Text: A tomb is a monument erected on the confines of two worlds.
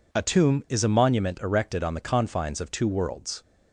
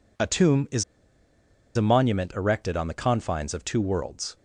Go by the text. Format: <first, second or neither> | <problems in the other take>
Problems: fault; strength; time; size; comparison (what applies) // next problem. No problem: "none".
first | pauses between "is" and "a"; noticeable; at 0.8 s; 0.93 s long